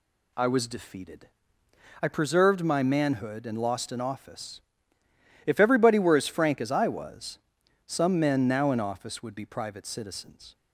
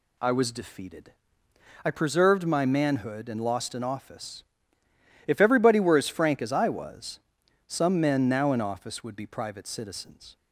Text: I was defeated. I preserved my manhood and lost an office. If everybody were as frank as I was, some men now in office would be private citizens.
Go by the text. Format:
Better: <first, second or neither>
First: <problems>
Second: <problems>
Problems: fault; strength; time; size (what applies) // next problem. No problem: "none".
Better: neither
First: none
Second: none